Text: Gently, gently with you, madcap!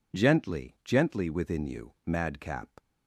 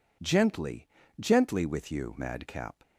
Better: second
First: says "within" for "with"; at 1.3 s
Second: none

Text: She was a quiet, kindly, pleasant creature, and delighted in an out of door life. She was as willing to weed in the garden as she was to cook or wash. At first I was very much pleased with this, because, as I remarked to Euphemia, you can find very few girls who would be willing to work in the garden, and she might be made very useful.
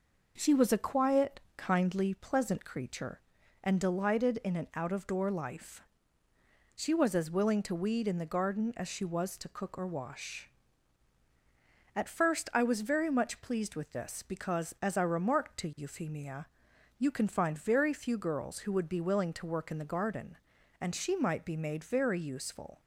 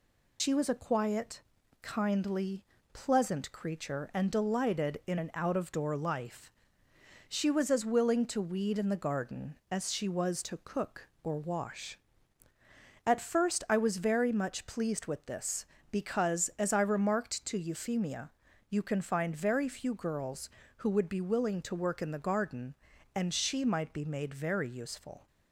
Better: first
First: none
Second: loses the start of "She"; at 0.3 s; 105 ms

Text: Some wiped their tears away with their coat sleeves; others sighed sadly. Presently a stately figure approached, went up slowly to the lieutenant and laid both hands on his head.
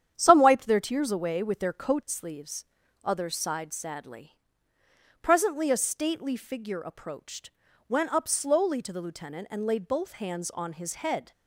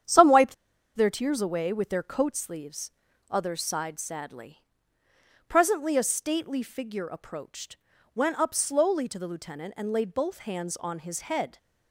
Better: first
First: starts louder than the rest; strong; until 1.1 s; 9 dB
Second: starts louder than the rest; strong; until 1.4 s; 9 dB // pauses between "wiped" and "their"; at 0.5 s; 0.40 s long

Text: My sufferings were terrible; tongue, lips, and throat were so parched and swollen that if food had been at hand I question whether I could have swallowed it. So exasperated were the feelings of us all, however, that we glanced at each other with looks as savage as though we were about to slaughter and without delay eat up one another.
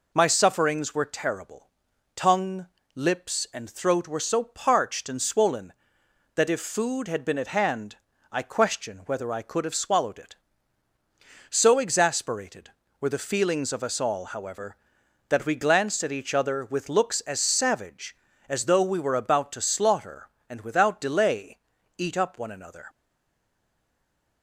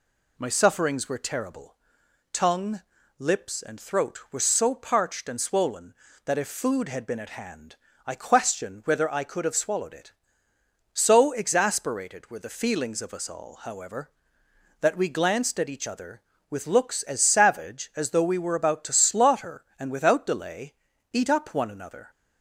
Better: second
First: pauses between "hand" and "I"; slight; at 7.9 s; 0.34 s long // pauses between "delay" and "eat"; at 21.5 s; 0.40 s long // stays silent after the last word; noticeable; from 22.8 s on; 1.6 s long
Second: pauses between "hand" and "I"; slight; at 7.7 s; 0.30 s long // pauses between "delay" and "eat"; at 20.7 s; 0.38 s long

